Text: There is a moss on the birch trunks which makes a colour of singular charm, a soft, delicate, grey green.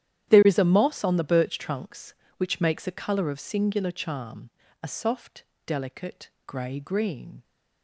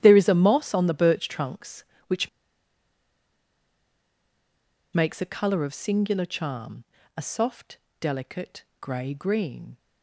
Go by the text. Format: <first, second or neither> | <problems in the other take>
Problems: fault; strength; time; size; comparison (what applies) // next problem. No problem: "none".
first | starts louder than the rest; strong; until 1.0 s; 11 dB; strong in the first // pauses between "which" and "makes"; strong; at 2.2 s; 2.6 s long